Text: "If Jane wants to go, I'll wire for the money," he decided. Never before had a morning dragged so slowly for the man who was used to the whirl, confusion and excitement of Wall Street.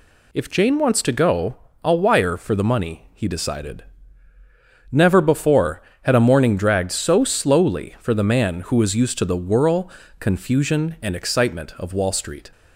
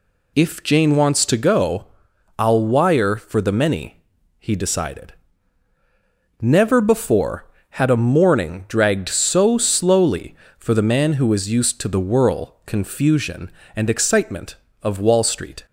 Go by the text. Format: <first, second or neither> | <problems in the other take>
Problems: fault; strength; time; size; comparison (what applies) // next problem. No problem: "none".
first | says "many" for "money"; at 3.5 s